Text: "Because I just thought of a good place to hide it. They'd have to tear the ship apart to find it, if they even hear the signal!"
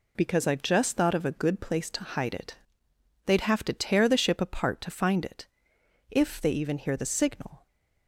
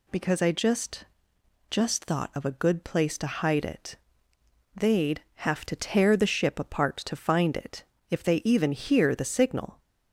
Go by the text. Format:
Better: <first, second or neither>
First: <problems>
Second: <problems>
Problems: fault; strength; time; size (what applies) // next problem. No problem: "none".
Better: first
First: none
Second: says "just" twice; at 1.6 s